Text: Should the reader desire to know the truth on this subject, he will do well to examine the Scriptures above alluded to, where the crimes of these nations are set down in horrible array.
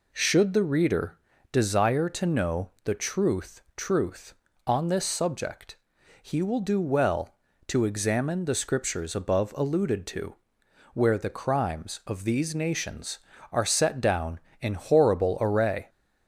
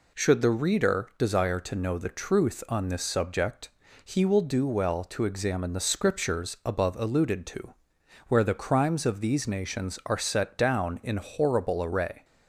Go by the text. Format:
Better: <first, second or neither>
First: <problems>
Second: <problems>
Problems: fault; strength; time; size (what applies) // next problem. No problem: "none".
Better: second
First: pauses between "reader" and "desire"; slight; at 1.1 s; 0.34 s long // pauses between "know" and "the"; slight; at 2.6 s; 0.16 s long // says "truth" twice; at 3.7 s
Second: none